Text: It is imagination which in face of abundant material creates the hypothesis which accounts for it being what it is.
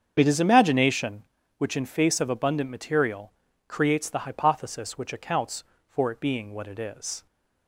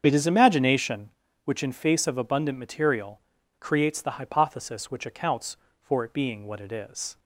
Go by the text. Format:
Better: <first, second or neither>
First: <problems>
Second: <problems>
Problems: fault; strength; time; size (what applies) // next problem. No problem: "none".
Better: neither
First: starts louder than the rest; strong; until 1.1 s; 7.5 dB // pauses between "material" and "creates"; slight; at 3.3 s; 0.34 s long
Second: starts louder than the rest; strong; until 1.0 s; 7.5 dB // pauses between "material" and "creates"; at 3.2 s; 0.37 s long